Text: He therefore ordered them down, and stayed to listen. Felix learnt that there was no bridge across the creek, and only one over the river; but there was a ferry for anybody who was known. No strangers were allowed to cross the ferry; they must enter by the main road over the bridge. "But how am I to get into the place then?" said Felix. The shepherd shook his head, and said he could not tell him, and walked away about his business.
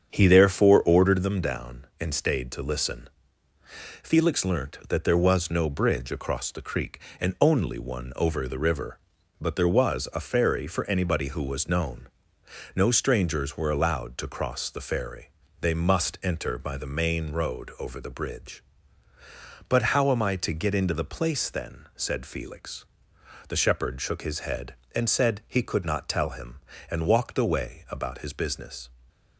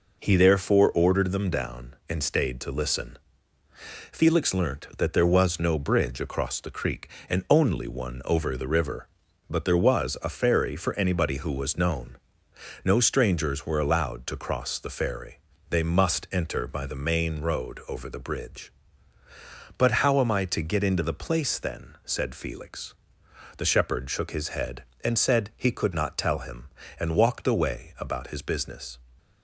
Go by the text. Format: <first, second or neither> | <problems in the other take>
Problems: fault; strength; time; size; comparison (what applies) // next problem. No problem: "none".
second | starts louder than the rest; strong; until 1.4 s; 7.5 dB